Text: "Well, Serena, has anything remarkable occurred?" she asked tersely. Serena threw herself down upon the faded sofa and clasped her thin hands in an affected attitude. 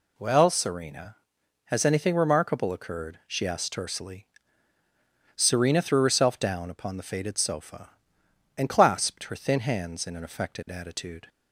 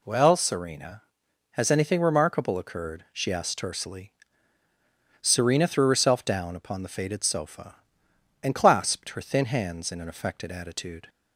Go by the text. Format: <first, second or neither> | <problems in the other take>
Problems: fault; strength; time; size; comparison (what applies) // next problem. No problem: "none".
neither | none